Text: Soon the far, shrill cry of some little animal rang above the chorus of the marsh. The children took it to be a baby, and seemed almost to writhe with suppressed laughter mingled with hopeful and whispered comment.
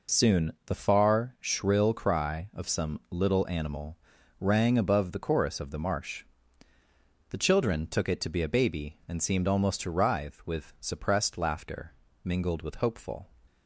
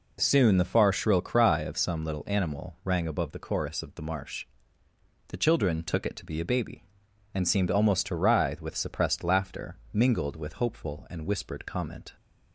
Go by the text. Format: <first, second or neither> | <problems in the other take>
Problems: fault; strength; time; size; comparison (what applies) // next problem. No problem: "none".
second | pauses between "animal" and "rang"; at 3.9 s; 0.44 s long // pauses between "laughter" and "mingled"; slight; at 11.9 s; 0.32 s long; slight in the second // stops before "and whispered comment"; at 13.4 s